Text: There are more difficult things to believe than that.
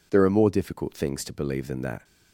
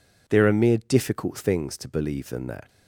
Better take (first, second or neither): first